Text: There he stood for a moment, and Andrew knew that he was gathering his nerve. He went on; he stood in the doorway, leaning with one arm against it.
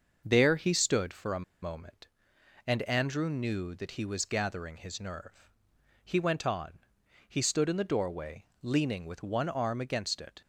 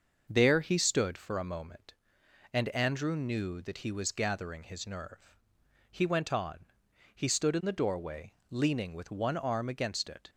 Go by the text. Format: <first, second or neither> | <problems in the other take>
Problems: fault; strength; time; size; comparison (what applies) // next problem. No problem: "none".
second | starts louder than the rest; until 1.2 s; 6 dB; also in the second // pauses between "a" and "moment"; slight; at 1.4 s; 0.19 s long